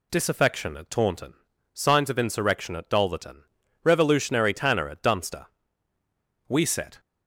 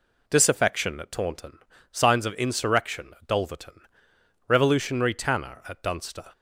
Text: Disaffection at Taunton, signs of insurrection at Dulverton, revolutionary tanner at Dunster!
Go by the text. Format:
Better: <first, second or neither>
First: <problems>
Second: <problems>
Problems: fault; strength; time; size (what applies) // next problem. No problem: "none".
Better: second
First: goes on to say "We set"; from 6.4 s on; 0.52 s long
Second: none